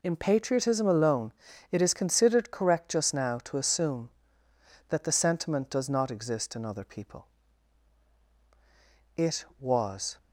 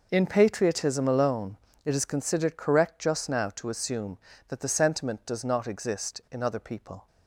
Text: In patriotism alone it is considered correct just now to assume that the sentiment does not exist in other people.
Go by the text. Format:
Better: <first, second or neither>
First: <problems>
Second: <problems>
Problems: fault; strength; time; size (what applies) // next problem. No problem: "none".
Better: second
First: pauses between "alone" and "it"; at 1.3 s; 0.38 s long // goes on to say "It was"; noticeable; from 9.1 s on; 1.0 s long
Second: pauses between "alone" and "it"; slight; at 1.5 s; 0.28 s long